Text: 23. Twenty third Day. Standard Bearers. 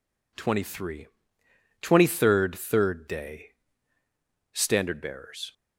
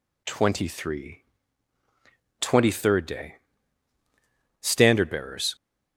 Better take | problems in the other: second | says "third" twice; at 2.5 s

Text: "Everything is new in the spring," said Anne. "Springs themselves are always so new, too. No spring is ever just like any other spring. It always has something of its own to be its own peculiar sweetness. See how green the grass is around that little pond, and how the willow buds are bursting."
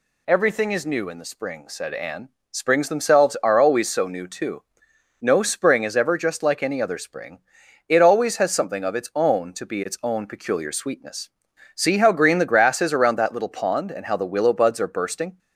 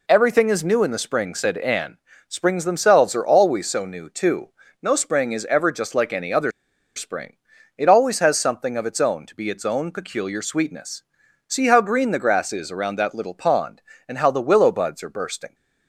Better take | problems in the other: first | pauses between "other" and "spring"; at 6.5 s; 0.45 s long

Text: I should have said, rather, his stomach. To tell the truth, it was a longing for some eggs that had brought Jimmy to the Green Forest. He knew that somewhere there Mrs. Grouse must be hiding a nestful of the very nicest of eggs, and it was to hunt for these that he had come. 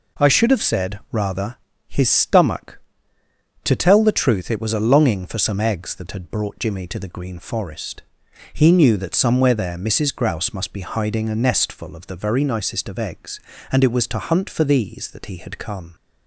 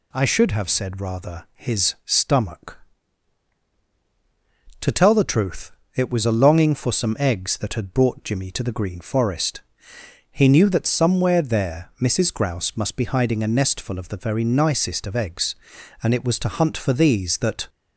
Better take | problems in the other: first | stops before "he had come"; at 17.6 s

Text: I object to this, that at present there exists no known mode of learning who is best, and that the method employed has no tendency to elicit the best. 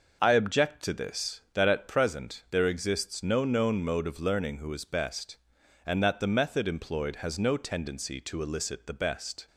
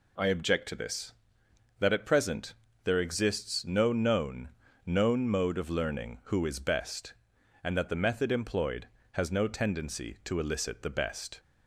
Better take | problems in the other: first | pauses between "present" and "there"; slight; at 2.5 s; 0.32 s long // says "known" twice; at 4.8 s

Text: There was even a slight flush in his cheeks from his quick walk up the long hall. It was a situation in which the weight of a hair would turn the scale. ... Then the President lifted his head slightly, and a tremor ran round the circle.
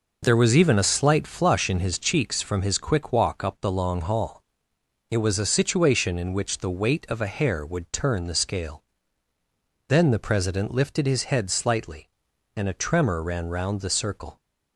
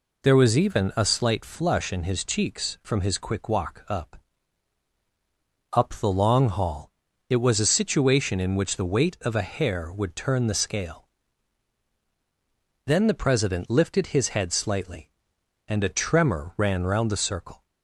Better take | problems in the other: first | says "up" twice; at 5.7 s

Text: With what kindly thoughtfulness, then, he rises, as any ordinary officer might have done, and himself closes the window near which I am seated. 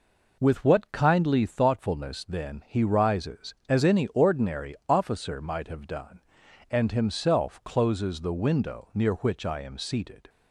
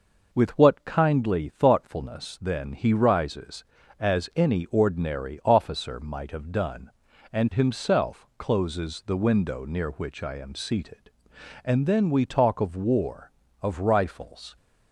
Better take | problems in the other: first | goes on to say "And then we talk of war of rifles"; strong; from 11.6 s on; 2.9 s long

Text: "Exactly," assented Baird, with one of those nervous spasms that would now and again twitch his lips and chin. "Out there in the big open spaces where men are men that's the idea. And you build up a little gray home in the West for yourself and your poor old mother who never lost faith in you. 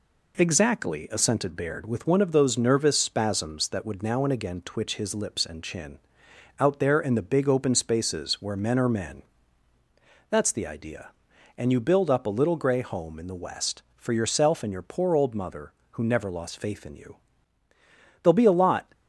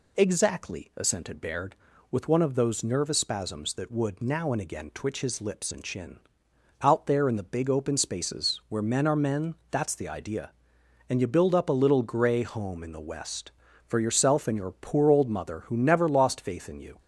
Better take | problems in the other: second | pauses between "men" and "that's"; at 9.2 s; 1.0 s long; slight in the second // goes on to say "There'll be a lot"; noticeable; from 18.2 s on; 0.68 s long

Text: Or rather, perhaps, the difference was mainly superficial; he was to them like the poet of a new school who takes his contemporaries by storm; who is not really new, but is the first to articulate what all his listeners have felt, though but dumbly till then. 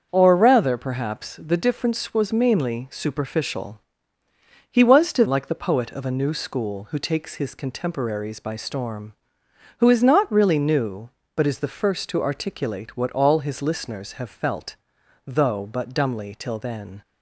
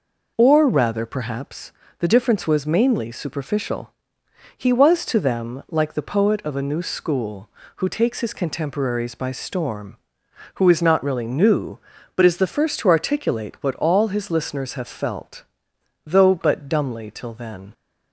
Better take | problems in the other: second | starts louder than the rest; until 1.1 s; 7 dB // skips "them"; at 5.2 s

